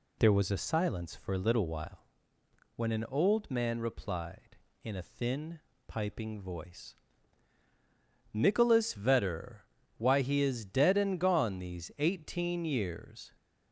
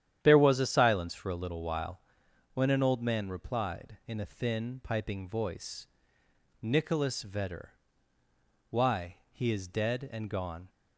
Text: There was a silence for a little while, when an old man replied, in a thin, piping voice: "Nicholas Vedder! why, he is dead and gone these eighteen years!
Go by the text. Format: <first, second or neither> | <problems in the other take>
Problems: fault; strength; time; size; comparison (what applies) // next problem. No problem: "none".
first | starts louder than the rest; strong; until 1.2 s; 10 dB // stops before "these eighteen years"; at 10.6 s